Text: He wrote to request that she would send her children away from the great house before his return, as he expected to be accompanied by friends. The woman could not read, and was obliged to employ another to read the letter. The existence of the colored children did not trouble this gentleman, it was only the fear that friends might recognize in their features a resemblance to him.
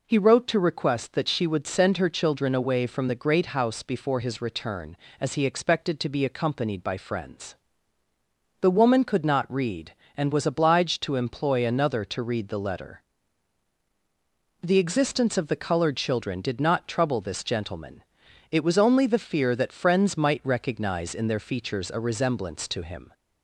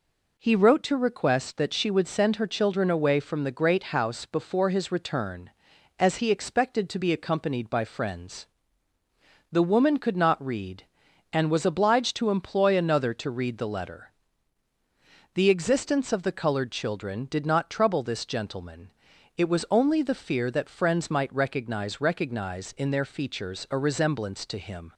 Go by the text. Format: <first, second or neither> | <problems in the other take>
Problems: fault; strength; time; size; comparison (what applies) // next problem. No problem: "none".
first | says "recognize" twice; at 21.9 s